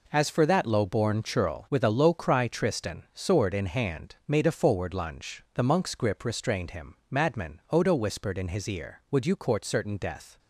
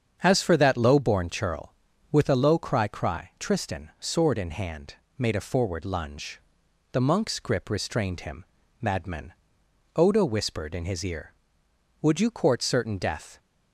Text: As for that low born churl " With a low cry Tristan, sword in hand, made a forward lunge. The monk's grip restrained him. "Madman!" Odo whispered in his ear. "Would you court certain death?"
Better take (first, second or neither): first